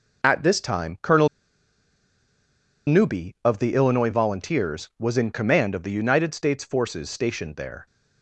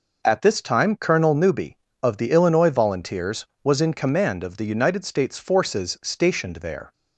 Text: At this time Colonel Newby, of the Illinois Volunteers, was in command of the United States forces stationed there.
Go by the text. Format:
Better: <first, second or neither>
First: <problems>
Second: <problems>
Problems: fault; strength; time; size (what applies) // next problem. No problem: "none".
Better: second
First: pauses between "Colonel" and "Newby"; strong; at 1.2 s; 1.5 s long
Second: none